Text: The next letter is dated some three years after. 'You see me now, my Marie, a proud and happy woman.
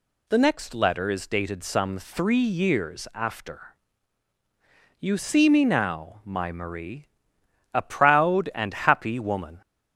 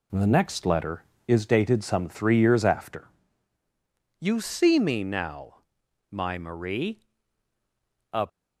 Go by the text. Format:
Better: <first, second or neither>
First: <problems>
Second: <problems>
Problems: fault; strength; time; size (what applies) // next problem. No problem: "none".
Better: first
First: none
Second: stops before "proud and happy woman"; at 8.2 s